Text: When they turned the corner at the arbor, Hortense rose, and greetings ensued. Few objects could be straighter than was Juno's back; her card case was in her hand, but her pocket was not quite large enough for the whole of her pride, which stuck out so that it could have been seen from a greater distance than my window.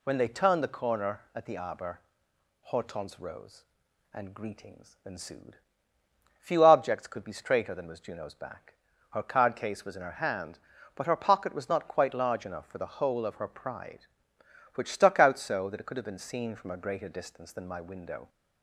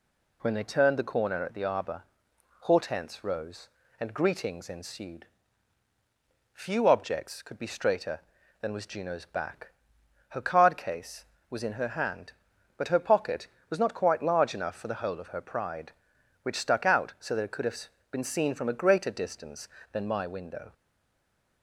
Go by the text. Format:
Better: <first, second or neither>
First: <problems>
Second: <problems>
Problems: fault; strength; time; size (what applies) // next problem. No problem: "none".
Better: first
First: none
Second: pauses between "have" and "been"; slight; at 17.8 s; 0.22 s long // stays silent after the last word; slight; from 20.7 s on; 0.9 s long